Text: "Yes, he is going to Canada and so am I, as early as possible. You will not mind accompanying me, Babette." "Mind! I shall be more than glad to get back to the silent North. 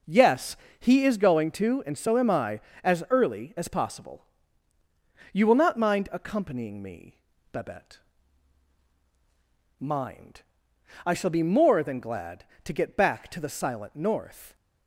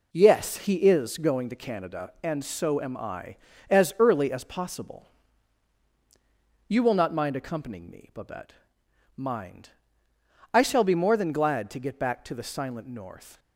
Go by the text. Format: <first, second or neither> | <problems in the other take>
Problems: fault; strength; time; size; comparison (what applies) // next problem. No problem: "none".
second | skips "Canada"; at 1.8 s